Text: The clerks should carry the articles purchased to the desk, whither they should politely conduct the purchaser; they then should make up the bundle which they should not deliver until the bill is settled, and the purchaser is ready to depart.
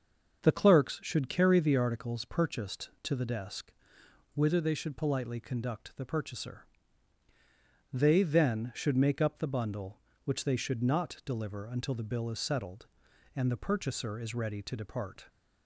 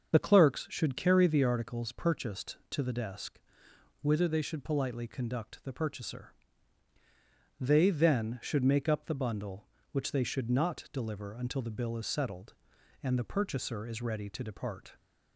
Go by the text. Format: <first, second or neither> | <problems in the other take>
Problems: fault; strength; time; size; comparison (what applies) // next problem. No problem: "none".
first | loses the start of "The"; at 0.1 s; 40 ms // starts louder than the rest; until 1.1 s; 7 dB; also in the first